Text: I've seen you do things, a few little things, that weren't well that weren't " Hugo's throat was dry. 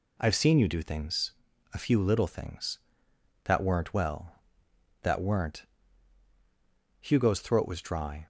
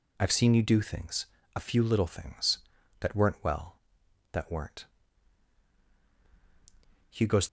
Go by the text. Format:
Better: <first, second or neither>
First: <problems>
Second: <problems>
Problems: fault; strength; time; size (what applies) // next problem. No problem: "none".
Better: first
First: none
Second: stops before "throat was dry"; at 7.4 s